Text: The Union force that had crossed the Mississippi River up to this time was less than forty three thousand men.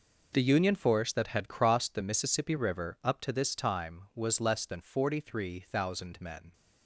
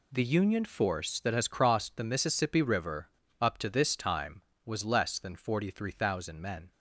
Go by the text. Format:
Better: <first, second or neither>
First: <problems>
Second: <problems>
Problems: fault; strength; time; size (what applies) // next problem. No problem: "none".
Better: first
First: none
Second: says "has" for "had"; at 1.3 s // pauses between "River" and "up"; slight; at 3.0 s; 0.29 s long